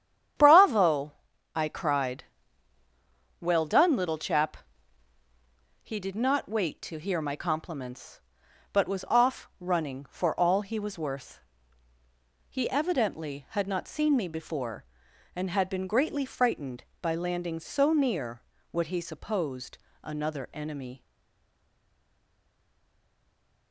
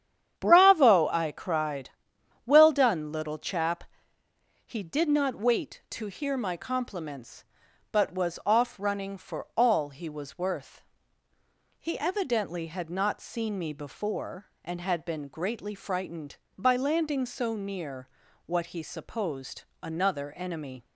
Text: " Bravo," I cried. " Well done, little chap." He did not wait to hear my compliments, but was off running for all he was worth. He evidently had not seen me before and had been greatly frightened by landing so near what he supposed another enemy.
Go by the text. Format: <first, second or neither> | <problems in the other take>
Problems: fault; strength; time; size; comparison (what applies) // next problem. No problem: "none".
second | starts louder than the rest; strong; until 1.8 s; 9 dB; strong in the second // pauses between "near" and "what"; slight; at 18.3 s; 0.30 s long; also in the second // pauses between "supposed" and "another"; slight; at 19.7 s; 0.24 s long; slight in the second // stays silent after the last word; strong; from 21.0 s on; 2.7 s long